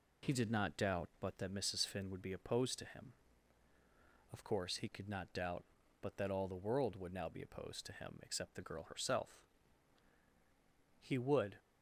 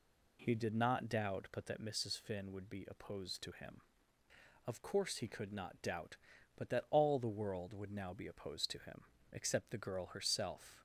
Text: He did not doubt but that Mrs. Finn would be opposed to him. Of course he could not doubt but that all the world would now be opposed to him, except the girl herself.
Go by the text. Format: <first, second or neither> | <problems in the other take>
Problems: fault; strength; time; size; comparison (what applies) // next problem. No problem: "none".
second | goes on to say "He would"; from 10.9 s on; 0.60 s long